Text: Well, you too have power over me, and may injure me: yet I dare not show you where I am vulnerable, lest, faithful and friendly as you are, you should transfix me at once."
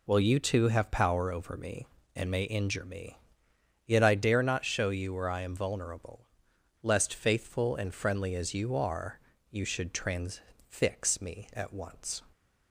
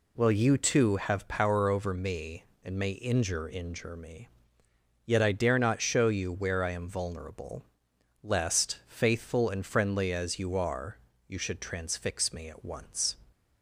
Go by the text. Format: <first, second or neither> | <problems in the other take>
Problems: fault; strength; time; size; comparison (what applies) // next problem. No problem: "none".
first | says "injure" twice; at 3.5 s